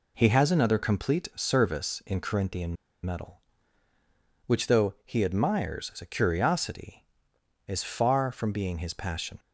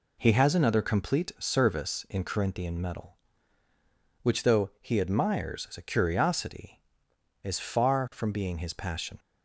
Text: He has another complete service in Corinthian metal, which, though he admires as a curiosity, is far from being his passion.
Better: second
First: pauses between "Corinthian" and "metal"; slight; at 2.7 s; 0.29 s long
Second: none

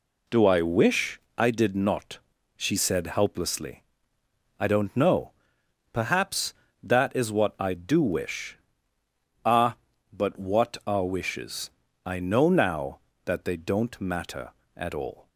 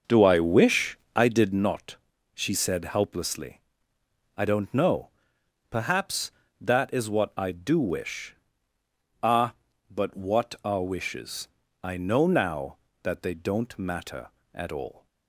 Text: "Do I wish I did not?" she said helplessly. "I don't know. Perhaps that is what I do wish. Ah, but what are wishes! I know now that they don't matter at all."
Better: first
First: pauses between "wish" and "I"; slight; at 1.2 s; 0.16 s long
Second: starts louder than the rest; noticeable; until 1.7 s; 6 dB // pauses between "wish" and "I"; slight; at 0.9 s; 0.16 s long

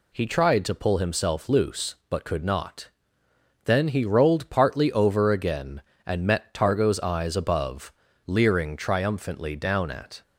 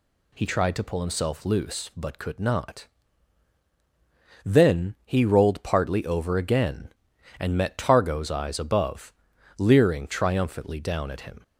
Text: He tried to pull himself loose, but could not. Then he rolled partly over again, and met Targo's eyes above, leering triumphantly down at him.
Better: second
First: stops before "him"; at 10.2 s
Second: none

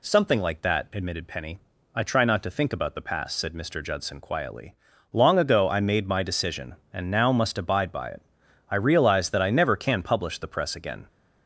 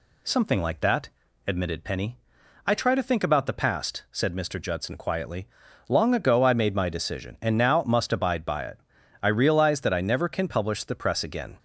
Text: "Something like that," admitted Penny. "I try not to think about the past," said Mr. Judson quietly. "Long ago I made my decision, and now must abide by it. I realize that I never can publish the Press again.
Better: first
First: none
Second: skips "not"; at 2.9 s

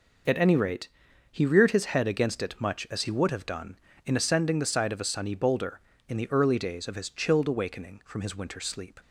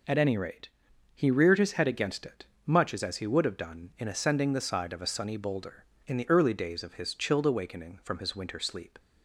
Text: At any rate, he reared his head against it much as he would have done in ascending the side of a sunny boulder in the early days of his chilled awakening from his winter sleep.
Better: first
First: none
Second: pauses between "it" and "much"; slight; at 2.4 s; 0.20 s long // says "as" twice; at 3.0 s

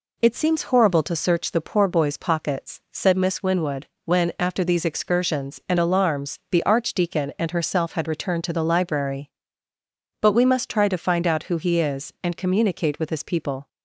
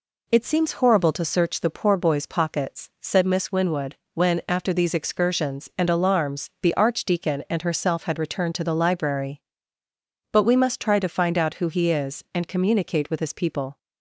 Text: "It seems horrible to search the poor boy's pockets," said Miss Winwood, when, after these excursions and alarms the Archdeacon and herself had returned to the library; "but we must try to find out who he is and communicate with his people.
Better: neither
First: none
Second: none

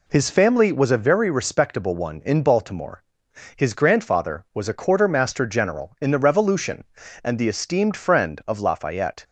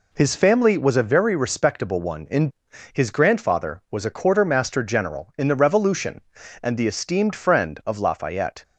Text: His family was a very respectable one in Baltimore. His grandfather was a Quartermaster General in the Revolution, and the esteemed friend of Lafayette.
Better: first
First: none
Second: skips "Baltimore"; at 2.7 s

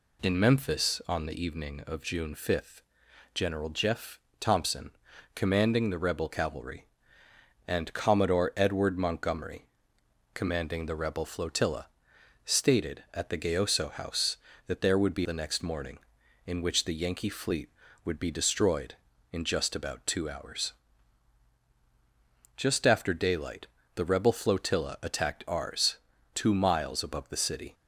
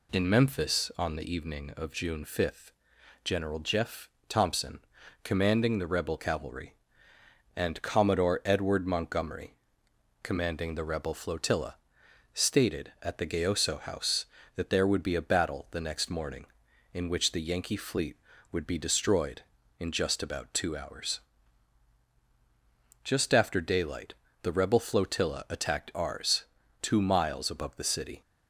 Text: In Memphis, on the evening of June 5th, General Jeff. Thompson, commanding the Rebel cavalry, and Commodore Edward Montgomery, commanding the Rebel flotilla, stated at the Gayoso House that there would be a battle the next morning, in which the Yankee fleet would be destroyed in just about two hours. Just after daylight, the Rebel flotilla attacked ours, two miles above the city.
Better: second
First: skips "a battle"; at 15.2 s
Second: none

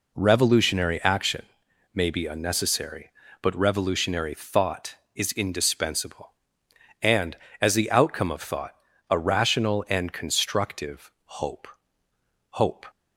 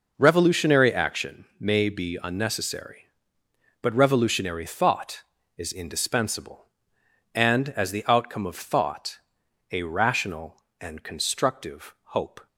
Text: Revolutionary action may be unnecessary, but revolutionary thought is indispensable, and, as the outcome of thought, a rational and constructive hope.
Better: second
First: pauses between "action" and "may"; noticeable; at 1.4 s; 0.50 s long // pauses between "constructive" and "hope"; slight; at 11.0 s; 0.16 s long // says "hope" twice; at 12.5 s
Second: pauses between "action" and "may"; slight; at 1.4 s; 0.16 s long

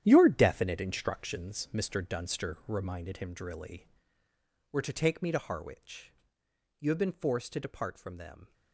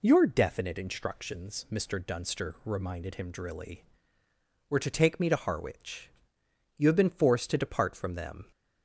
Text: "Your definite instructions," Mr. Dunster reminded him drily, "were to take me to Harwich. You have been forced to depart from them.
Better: second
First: gets quieter; strong; throughout; 12 dB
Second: none

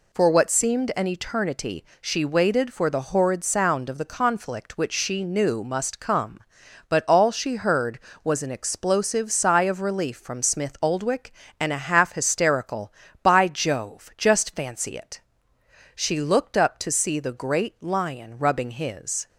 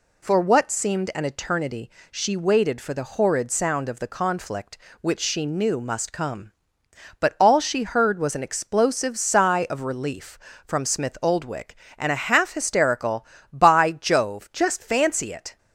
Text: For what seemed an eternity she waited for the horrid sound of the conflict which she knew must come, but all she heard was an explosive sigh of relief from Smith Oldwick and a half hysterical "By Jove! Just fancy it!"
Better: second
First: pauses between "eternity" and "she"; slight; at 1.8 s; 0.16 s long // goes on to say "She looked up to see the great lion rubbing his"; strong; from 15.9 s on; 3.3 s long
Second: pauses between "eternity" and "she"; slight; at 1.8 s; 0.20 s long

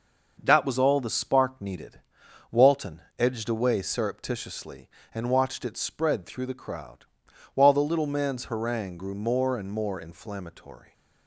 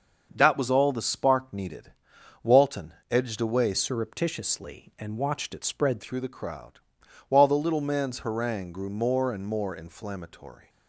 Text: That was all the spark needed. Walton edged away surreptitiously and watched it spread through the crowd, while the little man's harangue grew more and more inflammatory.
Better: first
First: starts louder than the rest; noticeable; until 1.4 s; 6 dB // pauses between "Walton" and "edged"; slight; at 3.0 s; 0.18 s long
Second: starts louder than the rest; until 1.3 s; 6.5 dB // pauses between "Walton" and "edged"; slight; at 2.9 s; 0.18 s long // changes voice from "surreptitiously" to "spread"; from 3.7 to 6.0 s; 2.3 s long

